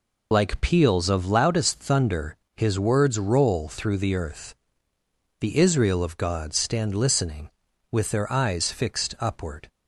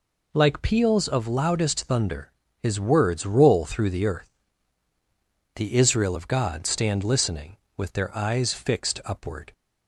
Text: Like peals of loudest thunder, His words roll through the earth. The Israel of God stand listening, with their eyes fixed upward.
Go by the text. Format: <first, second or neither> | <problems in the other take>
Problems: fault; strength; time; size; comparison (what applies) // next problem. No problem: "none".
second | loses the start of "Like"; at 0.3 s; 50 ms